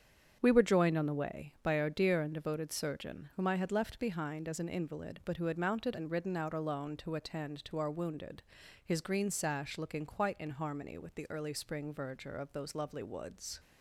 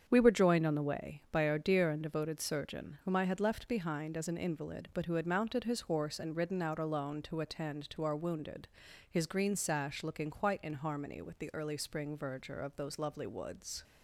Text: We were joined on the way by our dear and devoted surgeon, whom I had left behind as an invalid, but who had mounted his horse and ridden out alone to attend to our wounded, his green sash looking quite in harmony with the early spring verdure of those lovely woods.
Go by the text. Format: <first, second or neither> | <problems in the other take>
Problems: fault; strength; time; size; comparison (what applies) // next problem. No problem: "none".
second | starts louder than the rest; strong; until 1.4 s; 8 dB; strong in the second // skips "his horse"; at 5.9 s